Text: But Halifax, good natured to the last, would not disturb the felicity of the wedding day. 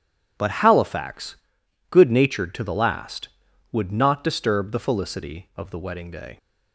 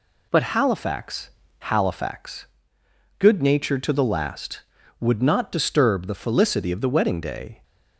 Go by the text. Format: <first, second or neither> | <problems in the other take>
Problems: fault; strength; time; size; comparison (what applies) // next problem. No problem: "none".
first | says "Halifax" twice; at 1.6 s